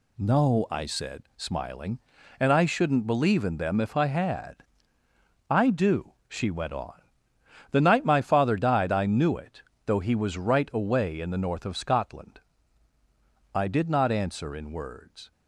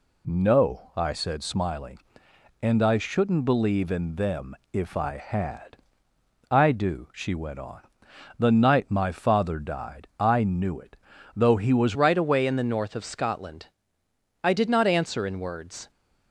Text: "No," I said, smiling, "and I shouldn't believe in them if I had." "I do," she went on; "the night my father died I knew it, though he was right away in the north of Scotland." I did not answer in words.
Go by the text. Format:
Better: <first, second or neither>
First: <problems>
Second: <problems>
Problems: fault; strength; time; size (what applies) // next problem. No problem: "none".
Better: first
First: none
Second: pauses between "them" and "if"; slight; at 4.5 s; 0.16 s long // changes voice at "right"; from 11.9 s on; 3.9 s long